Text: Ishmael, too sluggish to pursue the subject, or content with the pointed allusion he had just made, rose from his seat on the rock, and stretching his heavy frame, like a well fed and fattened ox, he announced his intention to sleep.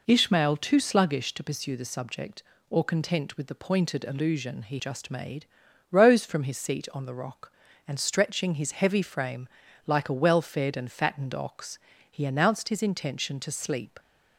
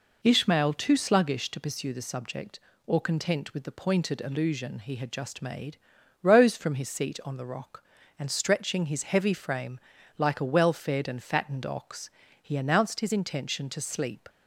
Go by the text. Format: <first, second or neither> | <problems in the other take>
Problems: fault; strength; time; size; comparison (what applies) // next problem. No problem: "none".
second | skips "had"; at 4.7 s